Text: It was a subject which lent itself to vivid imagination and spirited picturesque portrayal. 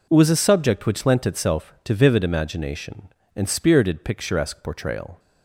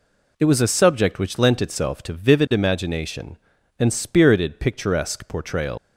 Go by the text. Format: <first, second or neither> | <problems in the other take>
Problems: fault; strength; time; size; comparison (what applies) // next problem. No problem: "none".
first | leaves "portrayal" unfinished; at 5.7 s; 105 ms